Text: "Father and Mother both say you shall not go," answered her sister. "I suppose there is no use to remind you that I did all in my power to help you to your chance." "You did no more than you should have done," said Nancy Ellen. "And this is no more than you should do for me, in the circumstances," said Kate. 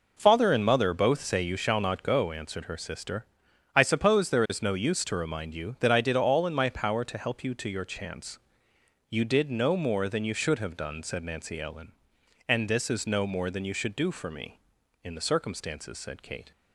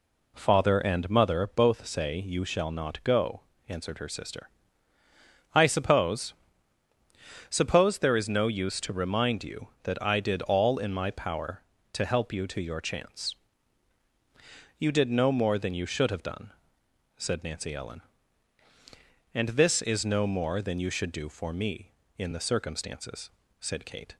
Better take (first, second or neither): first